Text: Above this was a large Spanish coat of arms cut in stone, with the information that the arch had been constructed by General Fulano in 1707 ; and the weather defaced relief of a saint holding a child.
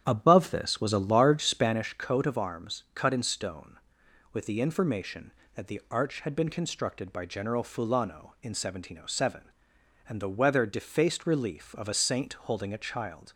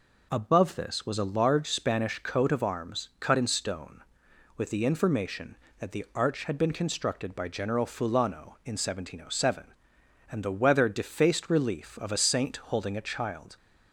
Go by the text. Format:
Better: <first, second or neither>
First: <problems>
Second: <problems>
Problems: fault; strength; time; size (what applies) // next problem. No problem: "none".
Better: second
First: starts louder than the rest; strong; until 1.8 s; 9.5 dB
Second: none